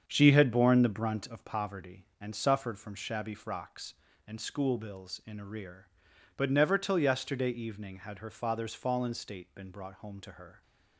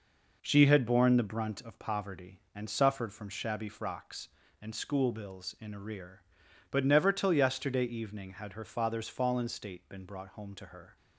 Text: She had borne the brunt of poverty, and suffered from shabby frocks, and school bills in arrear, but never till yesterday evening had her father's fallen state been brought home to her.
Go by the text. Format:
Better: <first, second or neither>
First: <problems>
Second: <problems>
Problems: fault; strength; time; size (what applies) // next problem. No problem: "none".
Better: second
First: starts louder than the rest; strong; until 1.7 s; 7.5 dB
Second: none